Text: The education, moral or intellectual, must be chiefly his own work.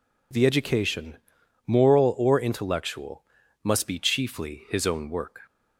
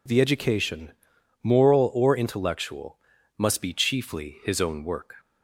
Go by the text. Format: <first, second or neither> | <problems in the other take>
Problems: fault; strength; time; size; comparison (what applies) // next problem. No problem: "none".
neither | none